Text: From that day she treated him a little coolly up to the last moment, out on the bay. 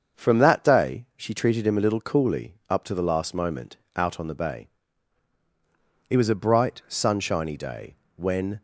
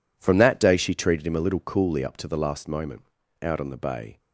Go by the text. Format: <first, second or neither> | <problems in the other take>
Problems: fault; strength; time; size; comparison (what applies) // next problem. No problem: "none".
second | starts louder than the rest; until 1.2 s; 7 dB // goes on to say "It was a bright sunshiny day when"; strong; from 6.0 s on; 2.5 s long